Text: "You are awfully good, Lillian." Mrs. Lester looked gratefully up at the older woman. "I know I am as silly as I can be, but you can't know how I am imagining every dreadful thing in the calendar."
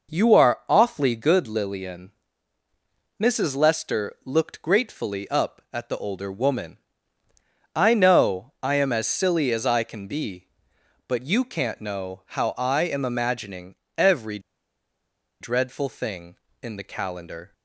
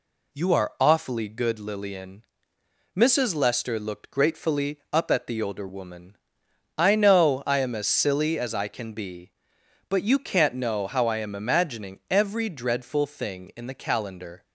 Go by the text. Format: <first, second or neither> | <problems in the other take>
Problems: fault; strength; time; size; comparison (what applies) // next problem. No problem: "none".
second | pauses between "imagining" and "every"; slight; at 13.7 s; 0.20 s long // pauses between "every" and "dreadful"; at 14.3 s; 1.0 s long